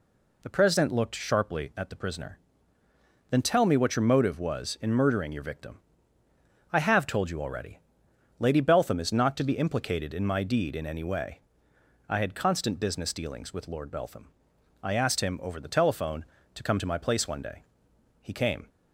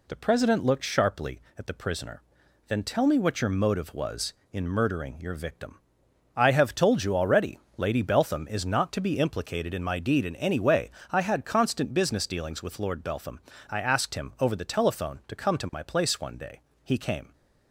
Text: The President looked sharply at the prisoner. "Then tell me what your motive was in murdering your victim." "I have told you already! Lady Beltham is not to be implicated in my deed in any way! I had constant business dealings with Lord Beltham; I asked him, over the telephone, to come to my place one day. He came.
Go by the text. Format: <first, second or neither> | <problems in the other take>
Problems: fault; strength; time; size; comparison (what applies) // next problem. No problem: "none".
neither | none